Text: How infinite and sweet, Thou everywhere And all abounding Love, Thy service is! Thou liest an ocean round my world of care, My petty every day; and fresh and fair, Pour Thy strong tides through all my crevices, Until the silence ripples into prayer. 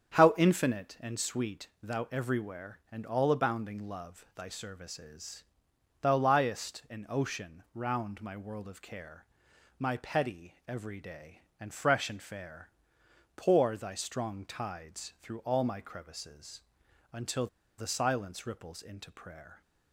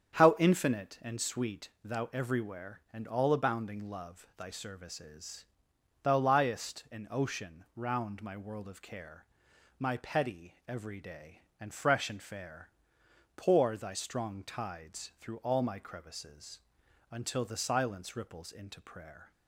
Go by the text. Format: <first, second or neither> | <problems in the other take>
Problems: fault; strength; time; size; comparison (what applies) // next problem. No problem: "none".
second | starts louder than the rest; strong; until 1.2 s; 8 dB; strong in the second // pauses between "petty" and "every"; slight; at 10.5 s; 0.16 s long; slight in the second // pauses between "Until" and "the"; slight; at 17.4 s; 0.31 s long